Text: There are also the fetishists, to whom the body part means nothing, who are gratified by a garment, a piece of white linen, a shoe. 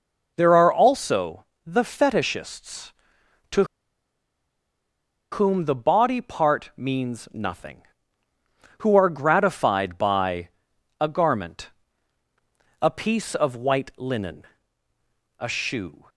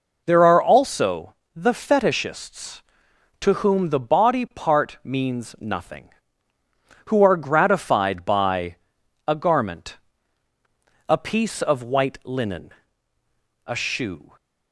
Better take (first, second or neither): second